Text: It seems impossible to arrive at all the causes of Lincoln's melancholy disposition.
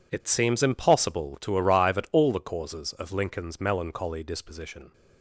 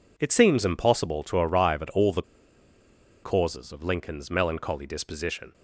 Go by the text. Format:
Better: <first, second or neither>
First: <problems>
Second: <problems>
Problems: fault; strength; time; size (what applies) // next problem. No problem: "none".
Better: first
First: none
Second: pauses between "the" and "causes"; at 2.2 s; 1.0 s long